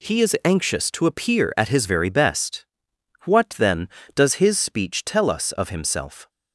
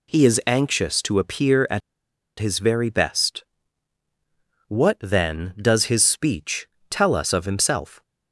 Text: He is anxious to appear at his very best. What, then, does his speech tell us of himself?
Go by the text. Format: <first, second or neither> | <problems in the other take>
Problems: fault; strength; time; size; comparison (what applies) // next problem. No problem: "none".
first | pauses between "at" and "his"; noticeable; at 1.8 s; 0.59 s long // pauses between "speech" and "tell"; slight; at 6.6 s; 0.24 s long